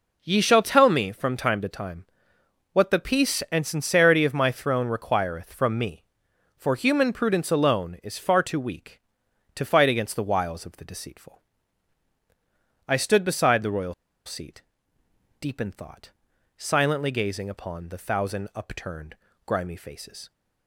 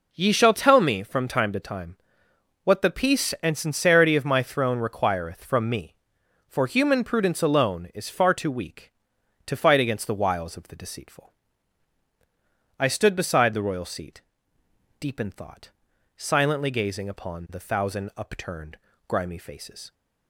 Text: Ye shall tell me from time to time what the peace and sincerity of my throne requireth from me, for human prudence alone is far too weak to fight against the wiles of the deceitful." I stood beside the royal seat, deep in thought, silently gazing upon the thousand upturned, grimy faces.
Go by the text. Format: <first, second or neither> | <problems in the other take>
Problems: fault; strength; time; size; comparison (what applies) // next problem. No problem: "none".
second | pauses between "time" and "what"; noticeable; at 2.0 s; 0.66 s long; noticeable in the second // pauses between "royal" and "seat"; slight; at 13.9 s; 0.32 s long